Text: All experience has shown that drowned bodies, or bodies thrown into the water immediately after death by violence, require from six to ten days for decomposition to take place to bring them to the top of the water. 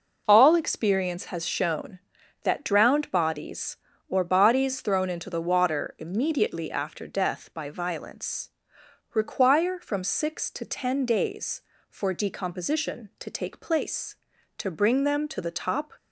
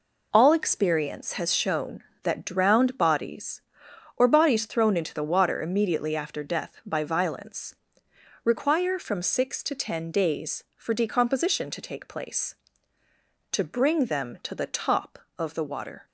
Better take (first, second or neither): second